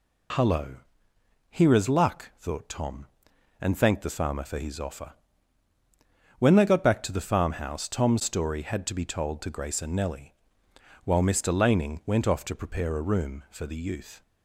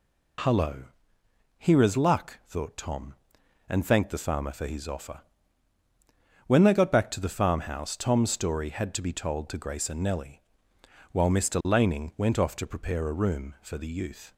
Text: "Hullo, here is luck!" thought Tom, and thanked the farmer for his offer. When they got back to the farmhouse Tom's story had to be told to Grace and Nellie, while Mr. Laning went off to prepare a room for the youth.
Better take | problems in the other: neither | none

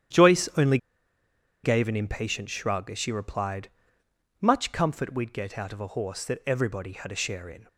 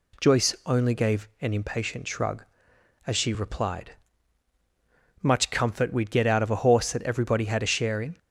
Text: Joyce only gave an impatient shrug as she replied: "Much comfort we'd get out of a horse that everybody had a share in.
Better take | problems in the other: second | starts louder than the rest; strong; until 2.0 s; 10 dB // pauses between "only" and "gave"; noticeable; at 0.7 s; 0.86 s long

